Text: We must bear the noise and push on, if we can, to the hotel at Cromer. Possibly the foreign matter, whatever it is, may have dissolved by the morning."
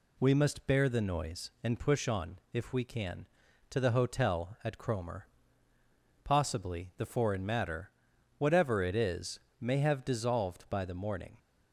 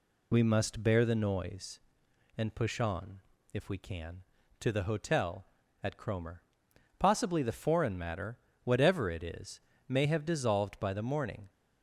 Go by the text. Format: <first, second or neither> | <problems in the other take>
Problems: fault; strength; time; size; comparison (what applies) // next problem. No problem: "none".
neither | none